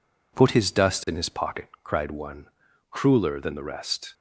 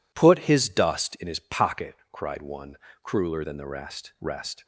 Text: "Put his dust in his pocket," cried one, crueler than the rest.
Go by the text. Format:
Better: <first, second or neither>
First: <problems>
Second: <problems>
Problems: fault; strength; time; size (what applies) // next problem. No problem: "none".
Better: first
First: none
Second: says "rest" twice; at 4.2 s